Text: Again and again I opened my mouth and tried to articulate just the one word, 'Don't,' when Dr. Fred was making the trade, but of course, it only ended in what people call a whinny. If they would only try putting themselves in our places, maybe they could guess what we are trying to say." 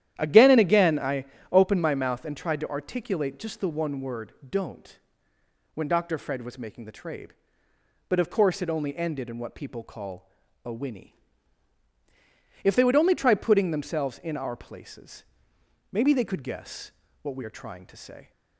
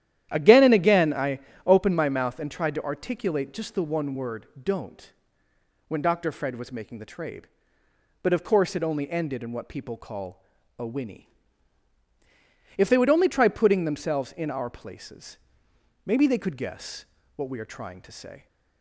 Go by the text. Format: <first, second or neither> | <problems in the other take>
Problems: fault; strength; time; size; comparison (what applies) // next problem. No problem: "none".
neither | starts louder than the rest; strong; the same in both // pauses between "I" and "opened"; slight; the same in both // pauses between "call" and "a"; slight; the same in both // pauses between "guess" and "what"; slight; the same in both